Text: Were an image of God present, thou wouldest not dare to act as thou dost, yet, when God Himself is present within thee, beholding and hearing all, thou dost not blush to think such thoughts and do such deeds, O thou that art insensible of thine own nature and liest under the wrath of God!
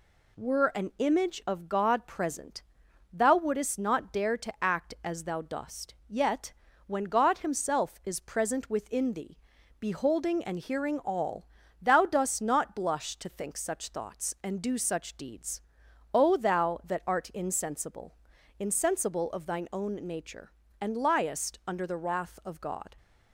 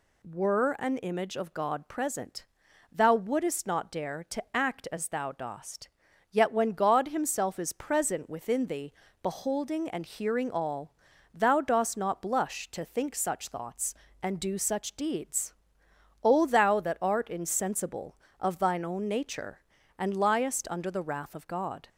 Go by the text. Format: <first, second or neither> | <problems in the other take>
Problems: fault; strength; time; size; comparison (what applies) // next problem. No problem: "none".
second | says "insensible" twice; at 18.5 s